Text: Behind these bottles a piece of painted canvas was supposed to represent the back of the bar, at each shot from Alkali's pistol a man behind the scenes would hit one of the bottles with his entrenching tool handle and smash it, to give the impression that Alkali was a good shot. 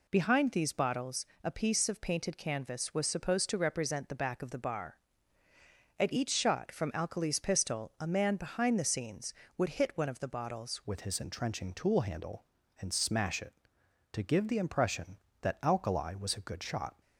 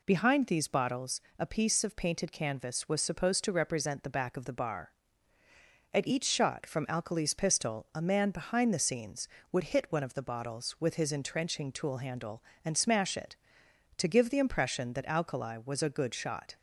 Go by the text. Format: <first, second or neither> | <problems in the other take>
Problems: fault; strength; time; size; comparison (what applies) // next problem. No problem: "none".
second | pauses between "bottles" and "a"; slight; at 1.2 s; 0.18 s long; slight in the second // changes voice at "with"; from 10.8 s on; 6.1 s long